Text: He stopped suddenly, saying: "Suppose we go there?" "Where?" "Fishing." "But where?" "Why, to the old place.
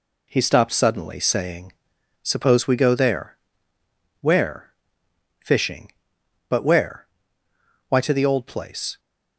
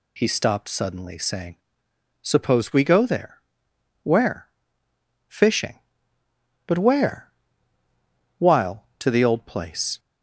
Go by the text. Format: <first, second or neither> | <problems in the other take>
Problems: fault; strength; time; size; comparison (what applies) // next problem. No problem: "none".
first | says "While" for "Why"; at 8.3 s